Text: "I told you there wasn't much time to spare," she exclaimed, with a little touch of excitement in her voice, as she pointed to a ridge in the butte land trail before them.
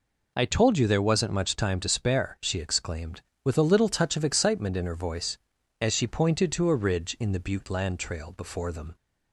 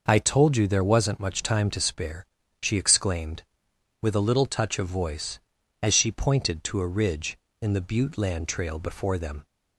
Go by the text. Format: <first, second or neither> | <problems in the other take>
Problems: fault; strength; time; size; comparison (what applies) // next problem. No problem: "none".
first | skips "excitement in her"; at 4.8 s